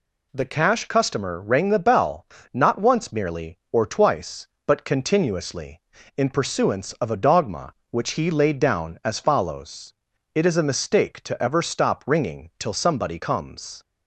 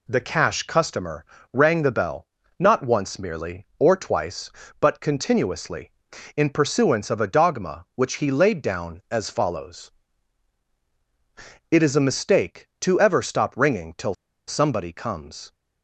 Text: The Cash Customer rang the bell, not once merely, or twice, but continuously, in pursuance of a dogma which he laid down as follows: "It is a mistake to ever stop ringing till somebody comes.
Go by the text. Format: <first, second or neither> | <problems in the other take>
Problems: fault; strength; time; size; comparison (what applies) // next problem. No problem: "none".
first | pauses between "Customer" and "rang"; slight; at 1.2 s; 0.26 s long // pauses between "till" and "somebody"; slight; at 14.1 s; 0.34 s long